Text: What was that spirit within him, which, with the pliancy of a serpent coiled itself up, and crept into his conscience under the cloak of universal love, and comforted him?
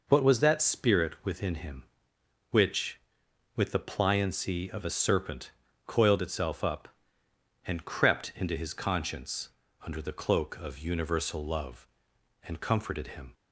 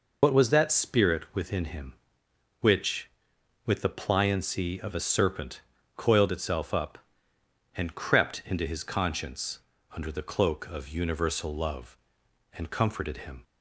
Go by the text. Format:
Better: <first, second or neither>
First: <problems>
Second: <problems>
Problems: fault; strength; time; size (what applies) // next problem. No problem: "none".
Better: first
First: pauses between "serpent" and "coiled"; slight; at 5.5 s; 0.34 s long // pauses between "conscience" and "under"; slight; at 9.4 s; 0.32 s long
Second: loses the start of "What"; at 0.2 s; 40 ms // pauses between "serpent" and "coiled"; slight; at 5.6 s; 0.34 s long // pauses between "conscience" and "under"; slight; at 9.5 s; 0.32 s long